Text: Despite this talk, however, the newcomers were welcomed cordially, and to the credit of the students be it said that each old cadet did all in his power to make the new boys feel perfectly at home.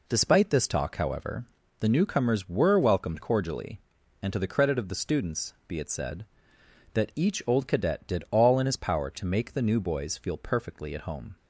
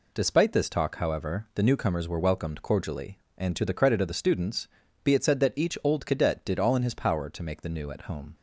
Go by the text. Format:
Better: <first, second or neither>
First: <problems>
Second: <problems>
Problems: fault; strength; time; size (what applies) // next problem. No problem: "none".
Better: first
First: none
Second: pauses between "students" and "be"; at 4.6 s; 0.38 s long // skips "boys feel perfectly"; at 7.9 s